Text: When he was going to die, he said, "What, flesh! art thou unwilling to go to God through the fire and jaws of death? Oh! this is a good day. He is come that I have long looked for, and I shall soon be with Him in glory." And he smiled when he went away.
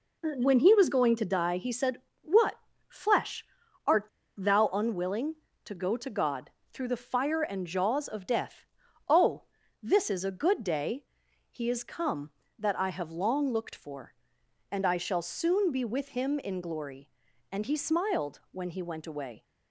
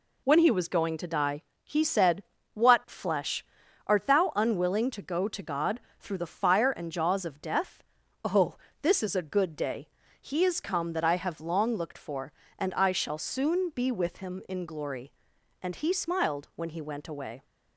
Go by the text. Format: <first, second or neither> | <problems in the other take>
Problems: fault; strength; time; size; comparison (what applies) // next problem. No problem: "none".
second | pauses between "art" and "thou"; slight; at 4.0 s; 0.31 s long // pauses between "God" and "through"; slight; at 6.5 s; 0.22 s long; slight in the second